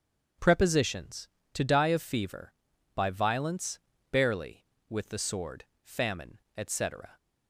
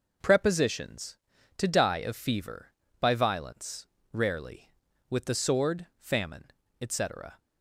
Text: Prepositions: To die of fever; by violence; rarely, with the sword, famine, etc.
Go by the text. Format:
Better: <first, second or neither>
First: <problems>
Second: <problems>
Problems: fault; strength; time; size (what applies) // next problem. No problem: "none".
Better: second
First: starts louder than the rest; strong; until 1.6 s; 7.5 dB // says "barely" for "rarely"; at 4.1 s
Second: none